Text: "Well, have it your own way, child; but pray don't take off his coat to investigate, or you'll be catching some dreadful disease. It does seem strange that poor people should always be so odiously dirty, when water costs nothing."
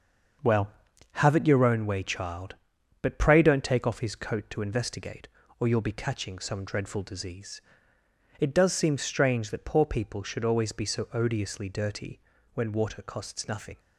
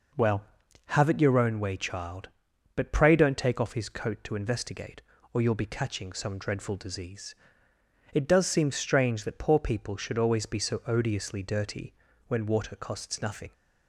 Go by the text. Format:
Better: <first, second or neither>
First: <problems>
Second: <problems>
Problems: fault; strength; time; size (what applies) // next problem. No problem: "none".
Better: second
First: gets quieter; throughout; 7 dB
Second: none